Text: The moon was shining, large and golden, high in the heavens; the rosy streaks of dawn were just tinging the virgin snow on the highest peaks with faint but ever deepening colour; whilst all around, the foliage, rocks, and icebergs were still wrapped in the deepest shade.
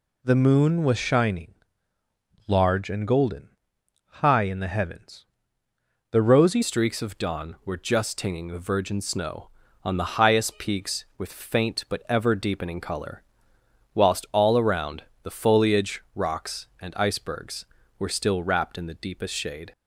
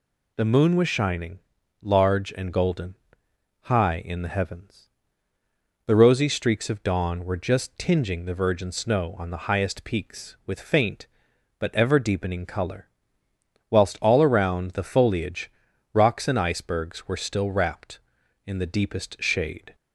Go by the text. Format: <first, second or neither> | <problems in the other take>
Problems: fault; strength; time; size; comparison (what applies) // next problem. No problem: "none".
second | changes voice at "streaks"; from 6.6 s on; 13.1 s long